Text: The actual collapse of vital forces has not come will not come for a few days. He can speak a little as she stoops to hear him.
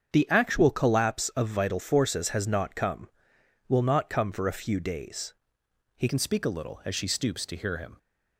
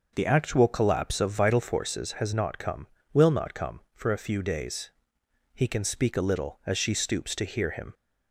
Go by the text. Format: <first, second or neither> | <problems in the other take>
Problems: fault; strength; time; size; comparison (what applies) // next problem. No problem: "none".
second | starts louder than the rest; strong; until 1.1 s; 7.5 dB // changes voice at "can"; from 6.0 s on; 1.9 s long